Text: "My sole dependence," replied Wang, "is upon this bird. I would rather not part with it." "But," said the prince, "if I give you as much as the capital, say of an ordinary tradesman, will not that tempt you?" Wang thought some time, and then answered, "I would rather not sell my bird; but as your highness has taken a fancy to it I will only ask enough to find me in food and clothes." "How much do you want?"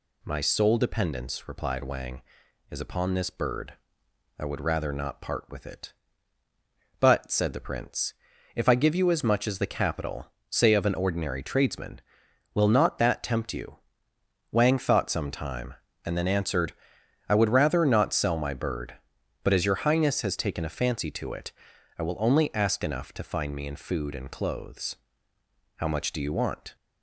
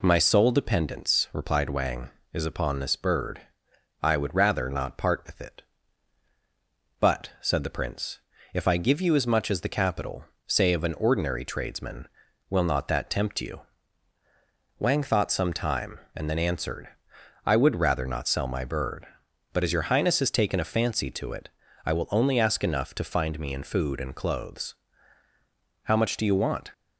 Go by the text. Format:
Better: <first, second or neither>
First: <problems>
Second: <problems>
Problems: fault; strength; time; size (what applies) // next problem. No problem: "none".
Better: neither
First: pauses between "it" and "I"; noticeable; at 21.5 s; 0.46 s long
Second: pauses between "it" and "I"; slight; at 21.4 s; 0.36 s long